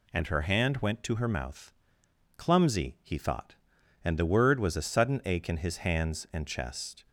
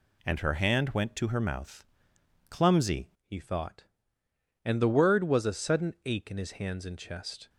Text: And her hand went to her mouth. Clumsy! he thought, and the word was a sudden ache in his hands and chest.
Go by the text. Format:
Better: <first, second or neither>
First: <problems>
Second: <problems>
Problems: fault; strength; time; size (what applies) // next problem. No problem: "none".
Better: first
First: none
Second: changes voice at "he"; from 3.2 s on; 4.2 s long